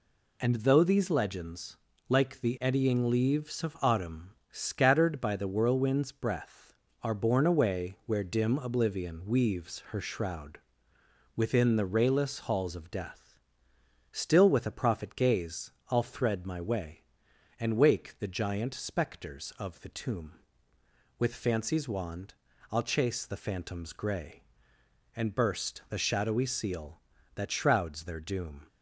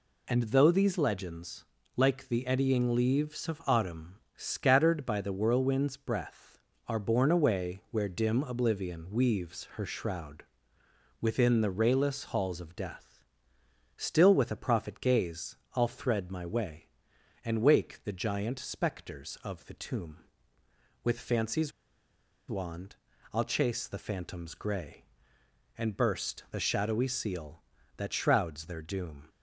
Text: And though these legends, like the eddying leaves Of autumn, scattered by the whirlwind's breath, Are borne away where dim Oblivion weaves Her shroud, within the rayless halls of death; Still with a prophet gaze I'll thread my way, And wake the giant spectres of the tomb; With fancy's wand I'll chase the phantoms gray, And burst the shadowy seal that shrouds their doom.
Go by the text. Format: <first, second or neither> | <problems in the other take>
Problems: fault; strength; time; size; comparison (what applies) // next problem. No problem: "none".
first | pauses between "gaze" and "I'll"; slight; at 15.5 s; 0.18 s long; slight in the first // pauses between "fancy's" and "wand"; noticeable; at 21.7 s; 0.79 s long // pauses between "wand" and "I'll"; slight; at 22.9 s; 0.36 s long; slight in the first